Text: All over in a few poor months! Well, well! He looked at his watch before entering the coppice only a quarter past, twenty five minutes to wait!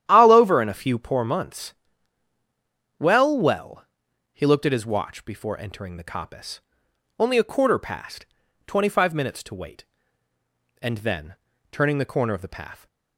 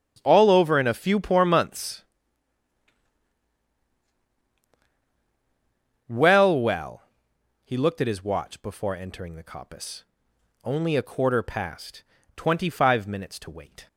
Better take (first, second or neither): second